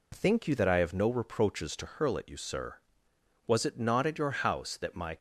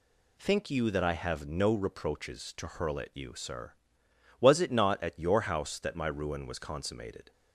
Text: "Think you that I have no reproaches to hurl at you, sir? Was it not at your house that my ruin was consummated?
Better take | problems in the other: second | stops before "ruin was consummated"; at 5.1 s

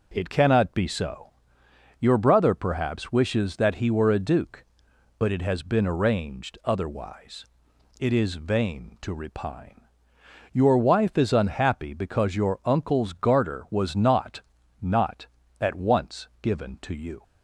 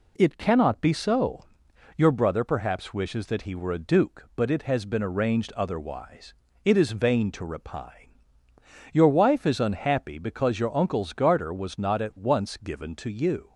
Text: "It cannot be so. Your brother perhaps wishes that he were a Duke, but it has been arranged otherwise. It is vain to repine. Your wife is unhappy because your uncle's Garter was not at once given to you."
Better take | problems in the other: second | says "not" twice; at 14.8 s

